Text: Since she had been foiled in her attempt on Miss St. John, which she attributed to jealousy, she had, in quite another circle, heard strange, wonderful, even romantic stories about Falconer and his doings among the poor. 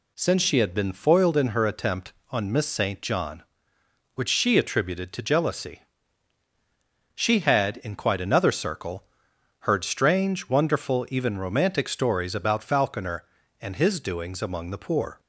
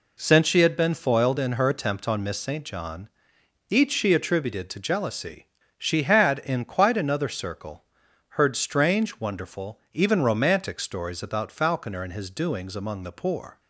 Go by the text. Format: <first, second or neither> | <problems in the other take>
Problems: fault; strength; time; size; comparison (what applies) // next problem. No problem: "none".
first | says "each" for "which"; at 3.6 s